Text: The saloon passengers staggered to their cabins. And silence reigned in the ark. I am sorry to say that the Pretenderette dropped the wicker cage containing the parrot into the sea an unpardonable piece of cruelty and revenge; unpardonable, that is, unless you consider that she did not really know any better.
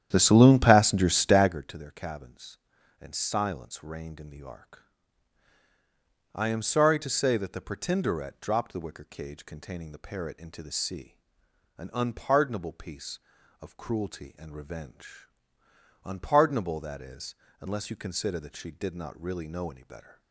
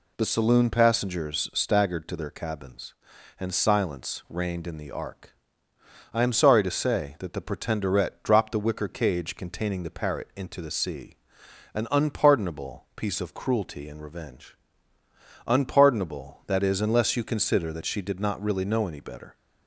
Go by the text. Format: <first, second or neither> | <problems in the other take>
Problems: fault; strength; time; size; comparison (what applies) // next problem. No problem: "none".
second | starts louder than the rest; strong; until 1.7 s; 10.5 dB // pauses between "sea" and "an"; noticeable; at 11.1 s; 0.62 s long; noticeable in the second